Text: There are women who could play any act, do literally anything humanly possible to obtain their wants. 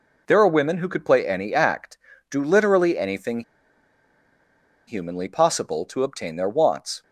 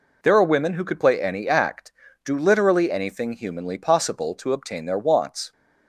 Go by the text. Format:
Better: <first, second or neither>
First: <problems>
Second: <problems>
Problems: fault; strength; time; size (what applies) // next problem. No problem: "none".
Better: second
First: pauses between "anything" and "humanly"; strong; at 3.4 s; 1.4 s long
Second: none